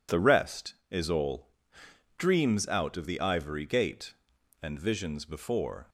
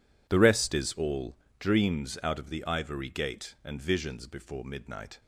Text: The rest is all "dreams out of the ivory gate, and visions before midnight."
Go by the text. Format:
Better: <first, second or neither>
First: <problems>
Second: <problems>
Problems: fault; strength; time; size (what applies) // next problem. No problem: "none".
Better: second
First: pauses between "all" and "dreams"; noticeable; at 1.4 s; 0.68 s long // stops before "midnight"; at 5.8 s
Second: pauses between "all" and "dreams"; slight; at 1.3 s; 0.20 s long